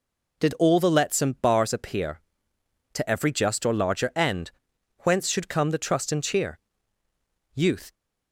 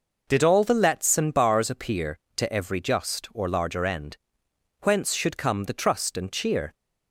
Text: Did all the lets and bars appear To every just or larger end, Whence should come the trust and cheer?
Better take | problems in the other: second | goes on to say "Youth"; slight; from 7.5 s on; 0.40 s long

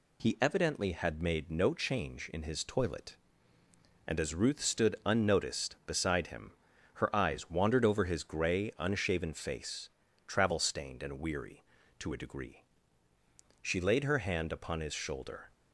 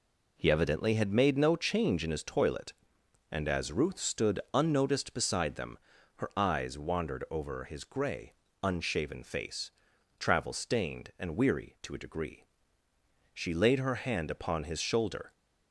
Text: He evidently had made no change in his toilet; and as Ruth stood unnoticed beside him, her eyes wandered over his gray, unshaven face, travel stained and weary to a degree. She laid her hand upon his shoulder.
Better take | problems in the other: first | says "them" for "him"; at 5.5 s

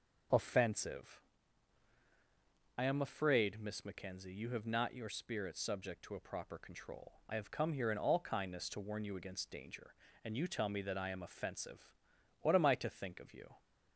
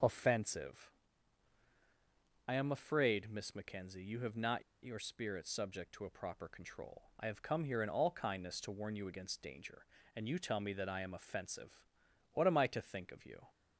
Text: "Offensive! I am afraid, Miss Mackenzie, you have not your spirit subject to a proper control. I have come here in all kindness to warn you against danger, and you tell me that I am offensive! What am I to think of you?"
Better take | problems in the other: first | pauses between "not" and "your"; slight; at 4.6 s; 0.22 s long

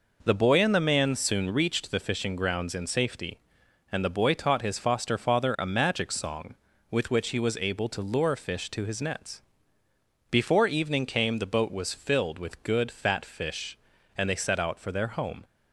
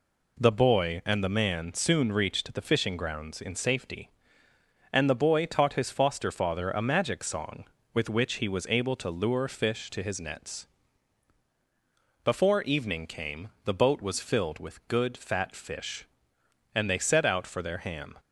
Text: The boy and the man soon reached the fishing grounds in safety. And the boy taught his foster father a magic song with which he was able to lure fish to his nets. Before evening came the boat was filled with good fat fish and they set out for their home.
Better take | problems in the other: first | pauses between "came" and "the"; slight; at 13.4 s; 0.16 s long // says "ham" for "home"; at 17.7 s

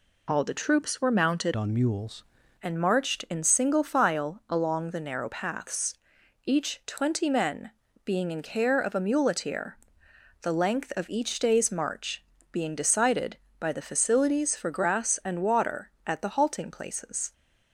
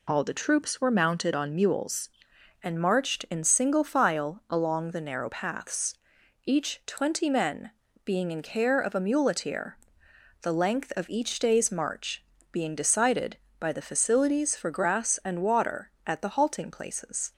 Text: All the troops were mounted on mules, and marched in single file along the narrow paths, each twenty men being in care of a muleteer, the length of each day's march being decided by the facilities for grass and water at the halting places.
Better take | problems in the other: second | changes voice from "on" to "mules"; from 1.5 to 2.2 s; 0.7 s long // pauses between "men" and "being"; slight; at 7.7 s; 0.32 s long; slight in the second // pauses between "march" and "being"; slight; at 12.2 s; 0.30 s long; slight in the second

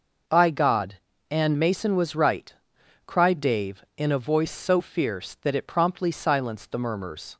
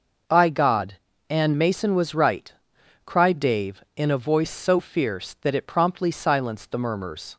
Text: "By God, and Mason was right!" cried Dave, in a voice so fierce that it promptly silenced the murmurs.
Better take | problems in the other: neither | none

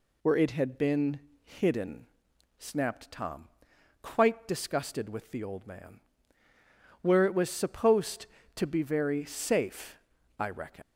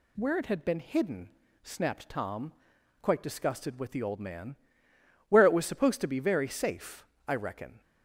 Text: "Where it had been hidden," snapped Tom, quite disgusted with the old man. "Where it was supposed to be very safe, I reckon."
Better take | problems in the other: second | pauses between "been" and "hidden"; slight; at 1.2 s; 0.24 s long // leaves "reckon" unfinished; at 10.8 s; 140 ms

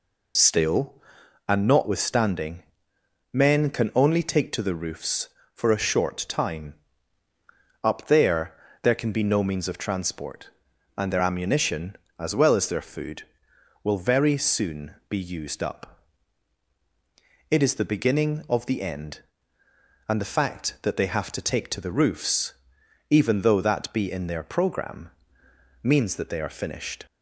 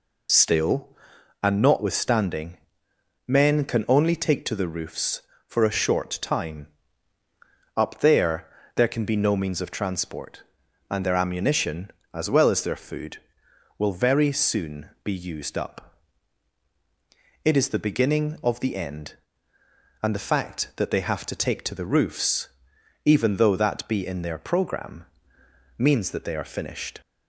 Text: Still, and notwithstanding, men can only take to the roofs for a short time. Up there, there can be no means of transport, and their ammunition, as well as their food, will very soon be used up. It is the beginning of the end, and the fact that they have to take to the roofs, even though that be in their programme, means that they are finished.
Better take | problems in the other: neither | none

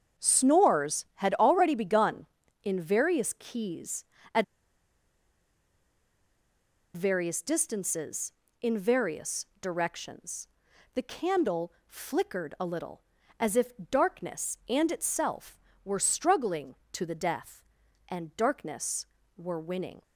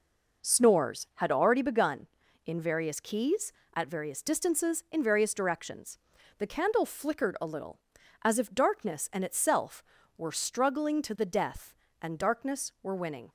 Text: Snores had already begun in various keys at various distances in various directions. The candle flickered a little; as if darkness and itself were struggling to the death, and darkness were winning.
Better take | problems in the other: second | starts louder than the rest; strong; until 1.2 s; 7.5 dB // pauses between "at" and "various"; strong; at 4.4 s; 2.5 s long // pauses between "if" and "darkness"; slight; at 13.7 s; 0.22 s long

